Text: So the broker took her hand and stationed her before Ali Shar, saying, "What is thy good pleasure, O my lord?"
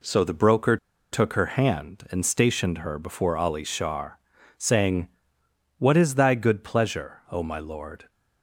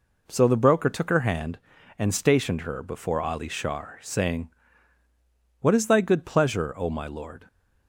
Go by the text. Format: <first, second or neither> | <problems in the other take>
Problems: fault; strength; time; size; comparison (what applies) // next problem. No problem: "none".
second | pauses between "broker" and "took"; slight; at 0.7 s; 0.36 s long